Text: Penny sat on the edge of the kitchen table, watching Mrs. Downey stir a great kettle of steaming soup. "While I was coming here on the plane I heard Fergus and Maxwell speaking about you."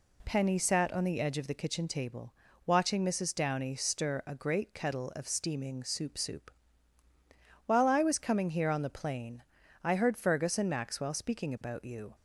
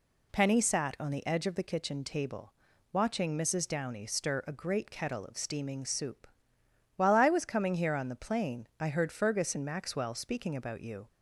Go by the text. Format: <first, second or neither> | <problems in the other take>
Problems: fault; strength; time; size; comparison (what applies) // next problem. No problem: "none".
second | says "soup" twice; at 6.1 s // pauses between "plane" and "I"; at 9.4 s; 0.42 s long